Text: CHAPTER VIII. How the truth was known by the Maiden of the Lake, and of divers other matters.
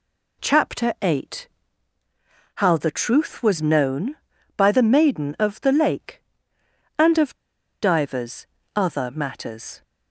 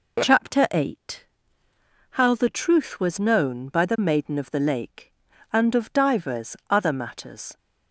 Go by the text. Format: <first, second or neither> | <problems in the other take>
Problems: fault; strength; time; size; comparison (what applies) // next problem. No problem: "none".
second | pauses between "of" and "divers"; noticeable; at 7.3 s; 0.46 s long // pauses between "divers" and "other"; slight; at 8.4 s; 0.28 s long